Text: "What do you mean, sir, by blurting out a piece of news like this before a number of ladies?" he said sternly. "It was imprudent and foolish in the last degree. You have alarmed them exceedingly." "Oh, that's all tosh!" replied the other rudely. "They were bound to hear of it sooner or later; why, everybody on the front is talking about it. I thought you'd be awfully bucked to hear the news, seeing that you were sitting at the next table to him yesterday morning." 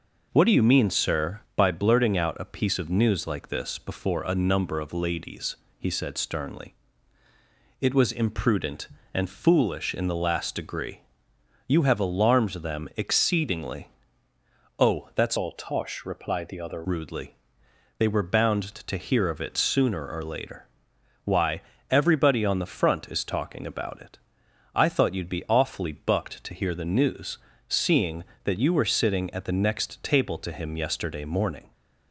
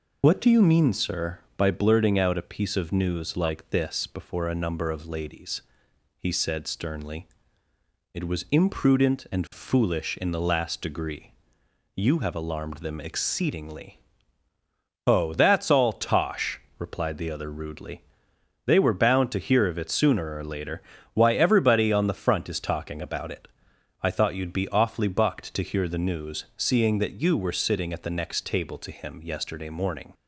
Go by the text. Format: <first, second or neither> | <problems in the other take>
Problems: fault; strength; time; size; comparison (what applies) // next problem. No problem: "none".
second | changes voice from "all" to "other"; from 15.3 to 16.8 s; 1.5 s long